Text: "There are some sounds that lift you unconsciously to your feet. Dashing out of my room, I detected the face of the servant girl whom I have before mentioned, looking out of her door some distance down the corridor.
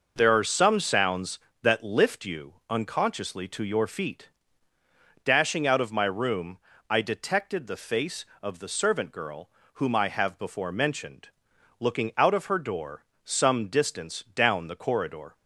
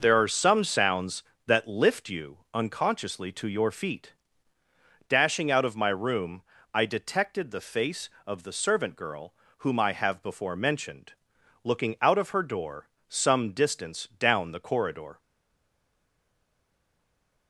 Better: first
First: pauses between "you" and "unconsciously"; slight; at 2.5 s; 0.16 s long // pauses between "girl" and "whom"; slight; at 9.5 s; 0.24 s long // pauses between "door" and "some"; slight; at 13.0 s; 0.22 s long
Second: pauses between "you" and "unconsciously"; slight; at 2.3 s; 0.16 s long // pauses between "girl" and "whom"; slight; at 9.3 s; 0.24 s long // pauses between "door" and "some"; slight; at 12.8 s; 0.22 s long // stays silent after the last word; from 15.1 s on; 2.3 s long

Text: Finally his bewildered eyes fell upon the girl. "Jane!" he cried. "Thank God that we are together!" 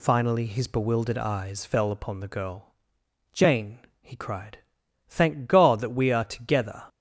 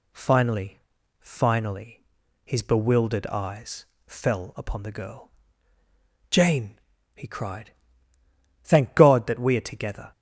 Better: first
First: none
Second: says "Finally" twice; at 1.1 s // pauses between "eyes" and "fell"; slight; at 3.8 s; 0.20 s long

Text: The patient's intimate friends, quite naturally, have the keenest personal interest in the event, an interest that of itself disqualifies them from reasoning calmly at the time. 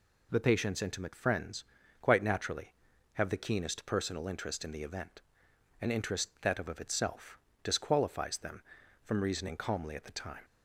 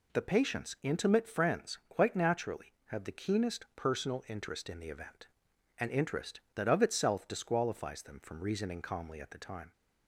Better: second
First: says "of" twice; at 6.6 s // pauses between "itself" and "disqualifies"; slight; at 7.3 s; 0.28 s long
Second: none

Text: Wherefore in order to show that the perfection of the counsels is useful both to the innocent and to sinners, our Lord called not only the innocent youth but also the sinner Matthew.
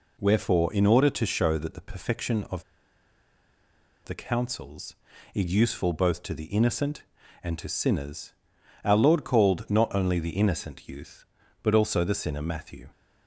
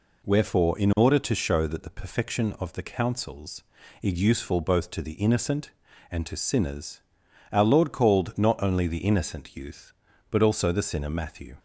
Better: second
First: pauses between "of" and "the"; strong; at 2.6 s; 1.4 s long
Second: none

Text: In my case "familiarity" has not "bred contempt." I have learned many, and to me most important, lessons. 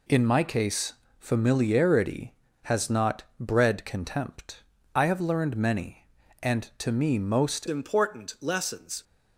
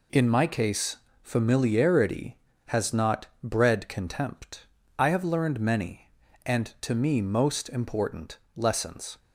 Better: second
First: pauses between "case" and "familiarity"; slight; at 0.9 s; 0.26 s long // pauses between "not" and "bred"; slight; at 3.2 s; 0.16 s long // changes voice at "important"; from 7.6 s on; 1.4 s long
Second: pauses between "case" and "familiarity"; slight; at 0.9 s; 0.26 s long // pauses between "not" and "bred"; slight; at 3.2 s; 0.16 s long

